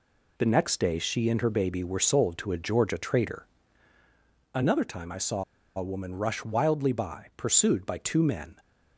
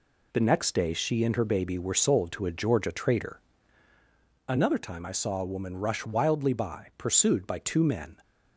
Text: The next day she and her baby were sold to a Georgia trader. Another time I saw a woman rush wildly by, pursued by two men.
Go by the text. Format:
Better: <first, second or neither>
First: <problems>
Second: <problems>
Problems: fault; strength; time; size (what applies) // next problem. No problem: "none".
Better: second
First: pauses between "saw" and "a"; slight; at 5.4 s; 0.34 s long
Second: none